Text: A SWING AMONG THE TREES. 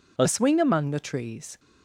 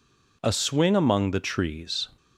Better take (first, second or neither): second